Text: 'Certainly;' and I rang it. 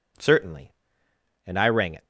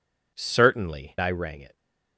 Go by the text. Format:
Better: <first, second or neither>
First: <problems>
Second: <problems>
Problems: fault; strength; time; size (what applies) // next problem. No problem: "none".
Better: first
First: none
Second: skips "and"; at 1.1 s